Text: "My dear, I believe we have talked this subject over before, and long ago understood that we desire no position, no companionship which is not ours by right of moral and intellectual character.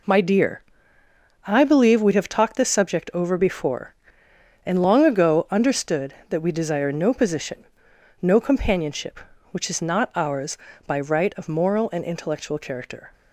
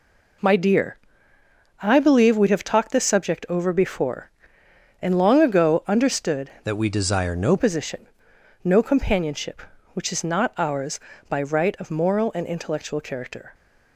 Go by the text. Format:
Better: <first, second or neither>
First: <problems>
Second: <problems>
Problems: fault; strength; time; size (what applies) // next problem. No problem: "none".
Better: first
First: none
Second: changes voice from "that" to "no"; from 6.6 to 7.5 s; 0.9 s long